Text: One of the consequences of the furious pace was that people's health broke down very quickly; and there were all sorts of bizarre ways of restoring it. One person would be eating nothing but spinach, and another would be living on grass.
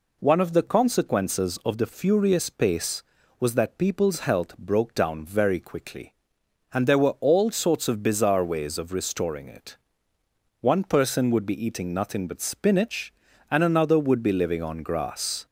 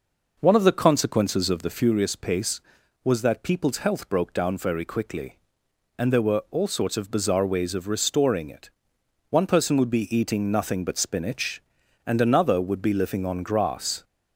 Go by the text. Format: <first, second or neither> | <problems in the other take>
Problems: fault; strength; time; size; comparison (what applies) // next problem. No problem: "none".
first | starts louder than the rest; noticeable; until 2.0 s; 5.5 dB